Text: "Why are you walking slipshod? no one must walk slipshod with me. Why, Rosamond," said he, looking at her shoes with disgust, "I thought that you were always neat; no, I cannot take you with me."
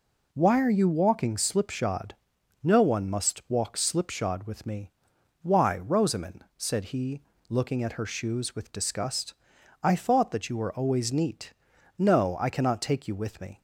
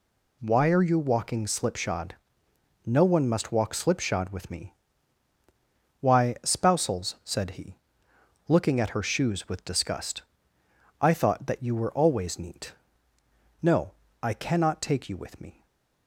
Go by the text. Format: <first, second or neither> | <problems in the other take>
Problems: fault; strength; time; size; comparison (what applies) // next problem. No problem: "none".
first | says "Spousals" for "Rosamond"; at 6.4 s // stays silent after the last word; slight; from 15.5 s on; 0.5 s long